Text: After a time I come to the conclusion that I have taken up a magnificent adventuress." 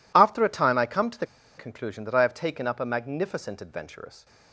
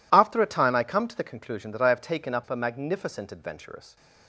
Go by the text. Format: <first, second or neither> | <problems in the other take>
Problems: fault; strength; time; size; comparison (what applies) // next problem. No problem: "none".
second | pauses between "the" and "conclusion"; slight; at 1.2 s; 0.30 s long